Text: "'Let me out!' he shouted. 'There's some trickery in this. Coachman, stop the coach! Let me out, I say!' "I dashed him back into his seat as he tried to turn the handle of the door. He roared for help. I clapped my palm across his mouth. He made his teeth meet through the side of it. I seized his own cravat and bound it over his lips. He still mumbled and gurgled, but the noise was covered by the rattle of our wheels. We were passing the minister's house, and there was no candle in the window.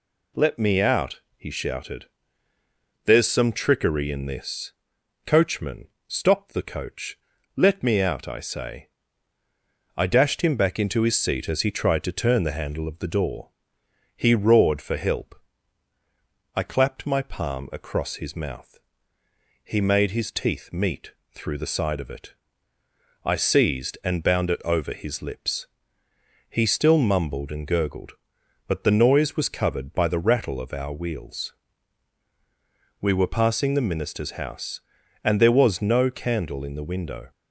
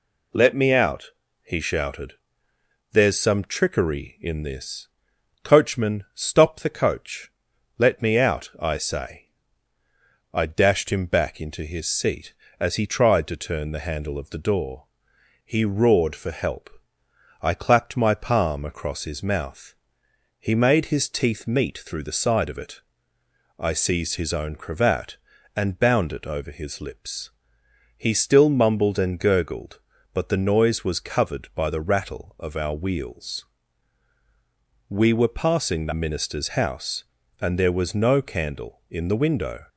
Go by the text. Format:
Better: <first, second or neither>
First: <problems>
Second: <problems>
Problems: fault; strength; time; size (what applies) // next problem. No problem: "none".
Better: second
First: pauses between "meet" and "through"; slight; at 21.1 s; 0.20 s long // skips "his own cravat"; at 24.0 s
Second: none